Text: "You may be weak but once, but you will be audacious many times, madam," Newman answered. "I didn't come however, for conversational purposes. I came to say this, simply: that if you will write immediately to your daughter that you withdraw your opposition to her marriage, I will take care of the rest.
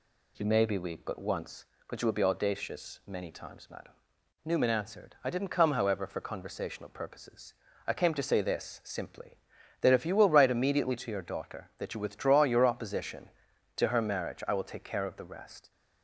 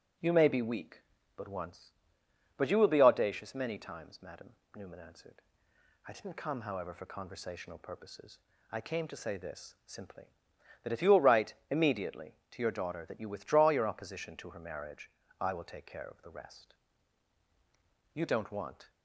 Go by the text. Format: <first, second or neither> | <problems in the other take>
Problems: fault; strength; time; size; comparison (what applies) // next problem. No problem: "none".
first | starts louder than the rest; strong; until 1.5 s; 10.5 dB // pauses between "write" and "immediately"; slight; at 11.5 s; 0.16 s long // goes on to say "You don't want"; noticeable; from 18.1 s on; 0.78 s long